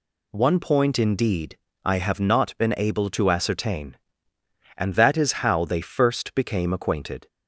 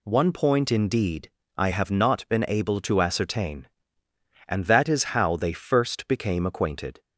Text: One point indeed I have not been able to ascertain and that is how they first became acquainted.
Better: neither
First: pauses between "indeed" and "I"; slight; at 1.5 s; 0.26 s long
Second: pauses between "indeed" and "I"; slight; at 1.3 s; 0.26 s long

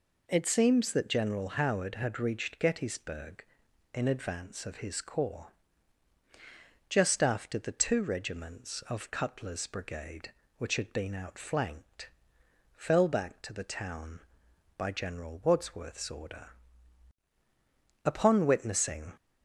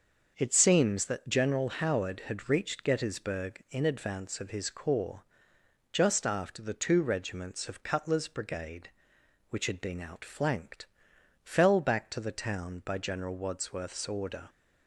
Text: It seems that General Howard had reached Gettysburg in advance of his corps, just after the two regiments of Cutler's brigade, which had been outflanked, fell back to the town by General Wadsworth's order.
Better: second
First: goes on to say "Upon witnessing"; noticeable; from 18.0 s on; 1.1 s long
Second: none

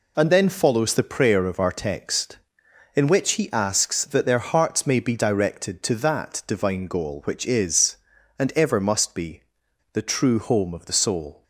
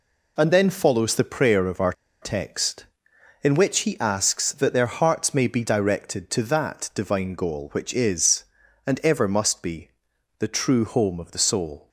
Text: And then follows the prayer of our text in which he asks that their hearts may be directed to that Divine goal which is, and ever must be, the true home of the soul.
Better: first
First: none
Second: pauses between "our" and "text"; slight; at 1.9 s; 0.27 s long

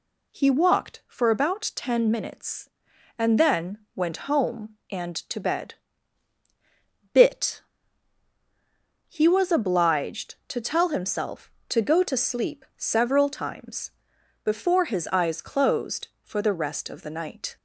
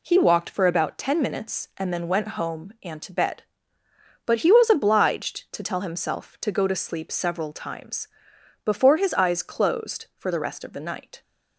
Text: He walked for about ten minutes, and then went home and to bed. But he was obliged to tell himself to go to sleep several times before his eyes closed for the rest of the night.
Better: second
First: pauses between "then" and "went"; slight; at 3.7 s; 0.18 s long // says "Bit" for "But"; at 7.1 s // pauses between "times" and "before"; noticeable; at 13.9 s; 0.54 s long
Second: pauses between "times" and "before"; noticeable; at 8.0 s; 0.56 s long

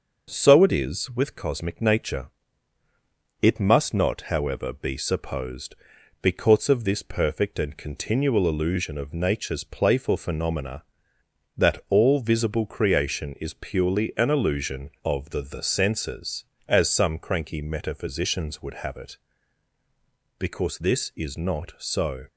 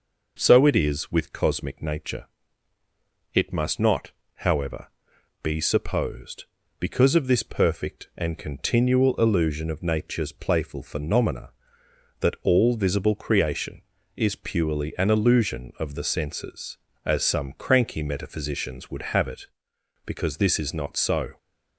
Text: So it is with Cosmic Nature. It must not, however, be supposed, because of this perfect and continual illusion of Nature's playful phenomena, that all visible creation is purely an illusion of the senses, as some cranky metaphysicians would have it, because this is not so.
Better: second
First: starts louder than the rest; noticeable; until 1.3 s; 6 dB // says "the" twice; at 15.4 s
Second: none

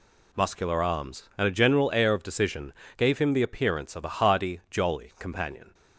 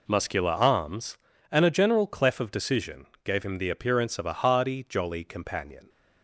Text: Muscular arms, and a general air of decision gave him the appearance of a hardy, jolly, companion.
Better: first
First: pauses between "decision" and "gave"; slight; at 2.7 s; 0.24 s long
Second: says "clef" for "air"; at 2.0 s // pauses between "decision" and "gave"; slight; at 3.0 s; 0.18 s long

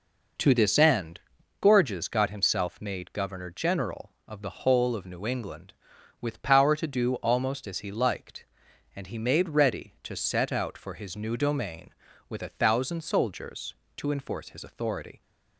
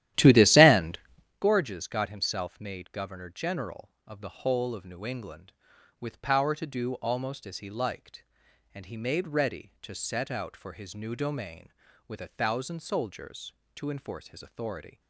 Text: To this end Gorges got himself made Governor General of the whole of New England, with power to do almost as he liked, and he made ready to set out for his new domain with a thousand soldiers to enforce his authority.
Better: first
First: pauses between "end" and "Gorges"; at 1.1 s; 0.41 s long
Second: starts louder than the rest; strong; until 1.4 s; 13 dB // pauses between "end" and "Gorges"; at 0.9 s; 0.42 s long

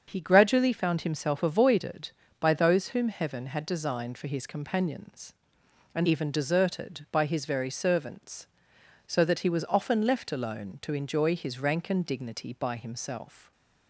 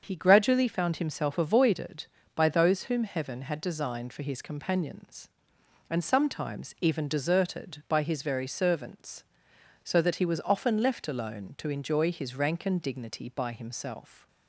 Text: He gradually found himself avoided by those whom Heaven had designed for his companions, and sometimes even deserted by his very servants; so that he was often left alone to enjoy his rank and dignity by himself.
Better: second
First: starts louder than the rest; strong; until 1.0 s; 7 dB // skips "sometimes"; at 6.0 s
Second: starts louder than the rest; until 1.0 s; 7 dB

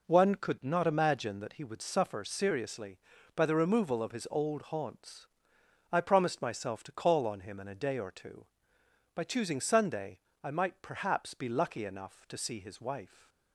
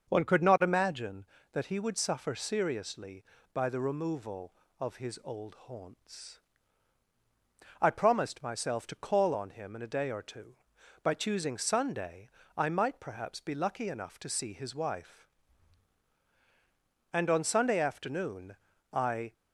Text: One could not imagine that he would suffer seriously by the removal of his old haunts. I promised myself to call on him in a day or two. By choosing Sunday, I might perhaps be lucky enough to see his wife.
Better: first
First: none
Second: starts louder than the rest; until 1.1 s; 6.5 dB // goes on to say "And on Sunday afternoon I"; strong; from 17.1 s on; 2.2 s long

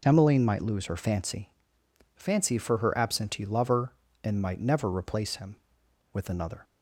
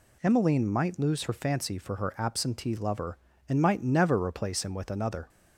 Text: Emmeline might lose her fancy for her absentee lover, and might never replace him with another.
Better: second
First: says "fancy" twice; at 2.1 s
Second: none

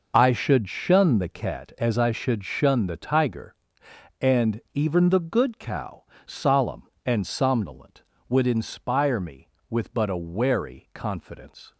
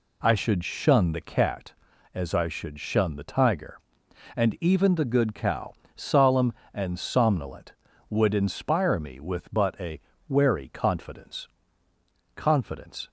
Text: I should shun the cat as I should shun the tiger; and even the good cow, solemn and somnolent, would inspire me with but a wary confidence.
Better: first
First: none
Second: pauses between "a" and "wary"; slight; at 9.9 s; 0.30 s long // says "confidence" twice; at 12.3 s

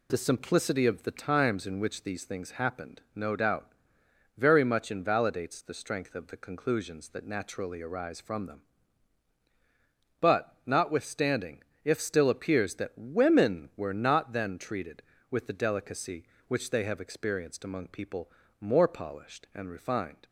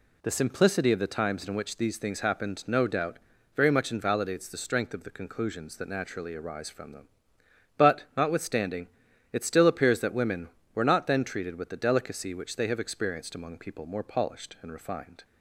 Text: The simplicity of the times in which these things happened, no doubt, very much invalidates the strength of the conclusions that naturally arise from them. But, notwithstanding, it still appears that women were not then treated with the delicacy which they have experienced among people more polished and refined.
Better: second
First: says "if" for "it"; at 11.8 s // pauses between "people" and "more"; slight; at 18.2 s; 0.30 s long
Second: none

